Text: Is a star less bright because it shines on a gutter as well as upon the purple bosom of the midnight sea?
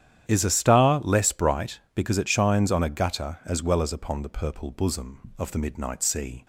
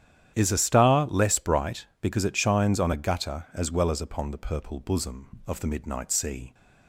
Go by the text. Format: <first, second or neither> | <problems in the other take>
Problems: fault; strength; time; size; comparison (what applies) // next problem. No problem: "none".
neither | starts louder than the rest; strong; the same in both